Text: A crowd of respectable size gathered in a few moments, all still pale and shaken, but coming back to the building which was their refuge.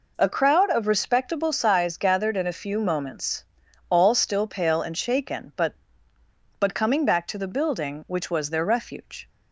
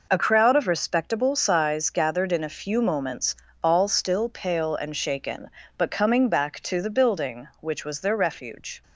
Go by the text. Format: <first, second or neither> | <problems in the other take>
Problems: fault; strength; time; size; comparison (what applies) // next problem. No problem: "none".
second | says "but" twice; at 6.6 s